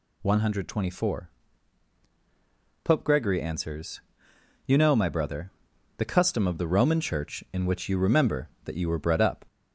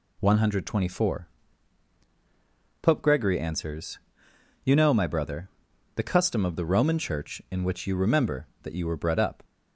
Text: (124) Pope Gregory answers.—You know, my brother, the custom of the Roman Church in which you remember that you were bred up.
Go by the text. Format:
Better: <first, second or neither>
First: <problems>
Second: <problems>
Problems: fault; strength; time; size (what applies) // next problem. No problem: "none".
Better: second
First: gets louder; slight; throughout; 2.5 dB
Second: none